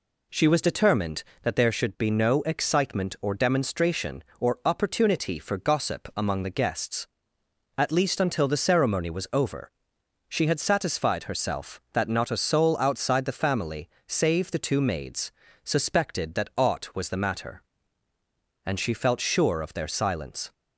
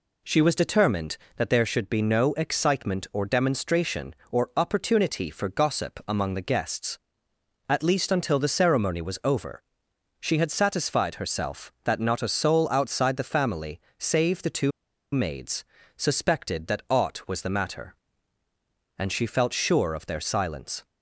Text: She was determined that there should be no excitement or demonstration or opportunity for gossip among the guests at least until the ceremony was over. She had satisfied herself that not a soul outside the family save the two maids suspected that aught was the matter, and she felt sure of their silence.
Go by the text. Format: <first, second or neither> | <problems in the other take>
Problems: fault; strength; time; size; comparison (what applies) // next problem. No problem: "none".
first | pauses between "family" and "save"; slight; at 13.8 s; 0.18 s long; slight in the first // pauses between "two" and "maids"; at 14.7 s; 0.42 s long // pauses between "maids" and "suspected"; slight; at 15.6 s; 0.34 s long; slight in the first